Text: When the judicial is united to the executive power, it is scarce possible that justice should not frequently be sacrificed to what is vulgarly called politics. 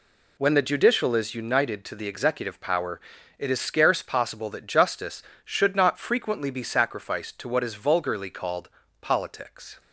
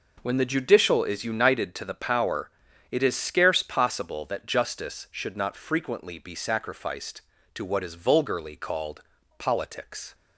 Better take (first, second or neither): first